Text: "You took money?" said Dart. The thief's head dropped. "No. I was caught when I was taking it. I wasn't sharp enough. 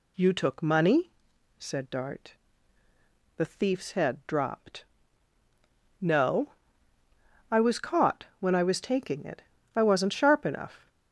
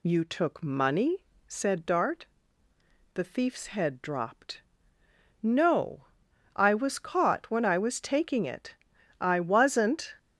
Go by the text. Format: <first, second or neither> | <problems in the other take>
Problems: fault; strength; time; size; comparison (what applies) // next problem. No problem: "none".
first | stops before "sharp enough"; at 10.1 s